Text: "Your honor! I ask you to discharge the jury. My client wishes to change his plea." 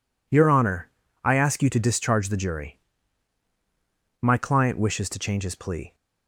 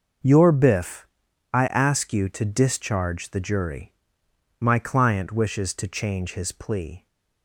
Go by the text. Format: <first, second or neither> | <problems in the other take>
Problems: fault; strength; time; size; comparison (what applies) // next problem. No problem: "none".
first | says "biff" for "honor"; at 0.5 s